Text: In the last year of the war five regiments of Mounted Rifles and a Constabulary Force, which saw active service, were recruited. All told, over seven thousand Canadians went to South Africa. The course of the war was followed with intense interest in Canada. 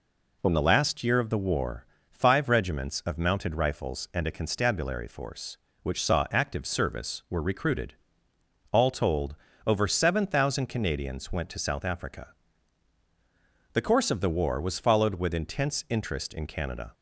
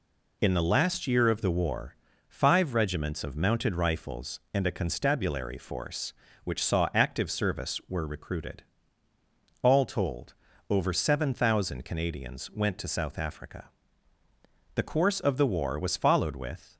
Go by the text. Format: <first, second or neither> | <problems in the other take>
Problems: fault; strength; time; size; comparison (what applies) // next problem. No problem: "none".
first | pauses between "war" and "five"; slight; at 1.9 s; 0.32 s long; slight in the first // stops before "intense interest in Canada"; at 16.7 s